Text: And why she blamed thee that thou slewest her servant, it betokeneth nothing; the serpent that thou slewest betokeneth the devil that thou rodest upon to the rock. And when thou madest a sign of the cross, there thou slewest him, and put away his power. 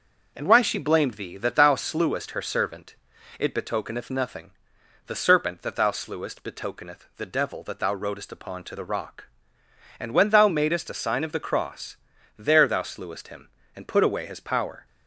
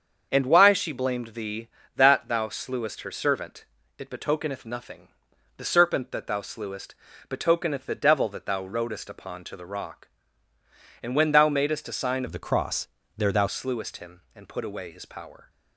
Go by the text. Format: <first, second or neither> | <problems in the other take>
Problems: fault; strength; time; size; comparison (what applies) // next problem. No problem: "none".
first | starts louder than the rest; until 1.3 s; 7 dB // pauses between "slewest" and "betokeneth"; slight; at 6.9 s; 0.34 s long // changes voice from "of" to "thou"; from 12.2 to 13.4 s; 1.2 s long